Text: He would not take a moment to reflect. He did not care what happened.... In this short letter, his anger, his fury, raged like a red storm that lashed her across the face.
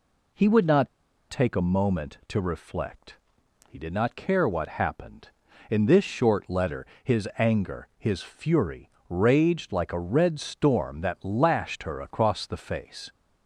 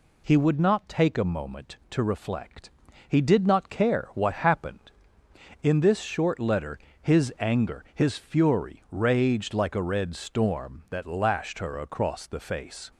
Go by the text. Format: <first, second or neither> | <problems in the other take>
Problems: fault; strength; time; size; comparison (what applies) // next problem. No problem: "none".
second | pauses between "not" and "take"; at 0.8 s; 0.41 s long